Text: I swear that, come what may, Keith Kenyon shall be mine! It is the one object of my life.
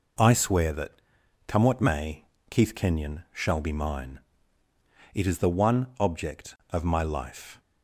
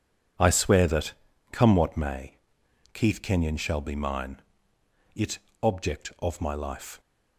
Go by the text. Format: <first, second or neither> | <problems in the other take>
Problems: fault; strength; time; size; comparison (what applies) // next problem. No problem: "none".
first | skips "is the one"; at 5.4 s